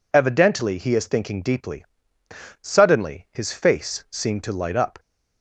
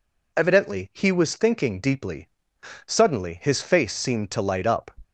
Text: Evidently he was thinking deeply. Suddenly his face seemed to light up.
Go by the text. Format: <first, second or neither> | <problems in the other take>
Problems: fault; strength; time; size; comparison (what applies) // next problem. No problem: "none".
second | says "is" for "was"; at 0.9 s